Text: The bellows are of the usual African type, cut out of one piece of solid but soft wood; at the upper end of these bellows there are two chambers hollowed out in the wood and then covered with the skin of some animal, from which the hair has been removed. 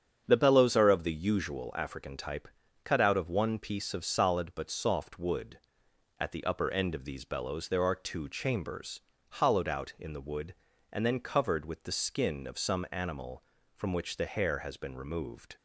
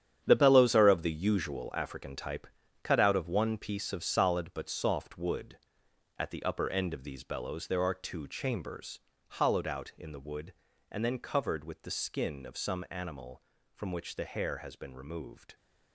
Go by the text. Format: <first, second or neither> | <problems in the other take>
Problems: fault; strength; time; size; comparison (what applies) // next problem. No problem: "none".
first | gets quieter; strong; throughout; 10.5 dB // starts louder than the rest; strong; until 1.2 s; 9 dB; strong in the first // pauses between "chambers" and "hollowed"; slight; at 9.0 s; 0.30 s long; slight in the first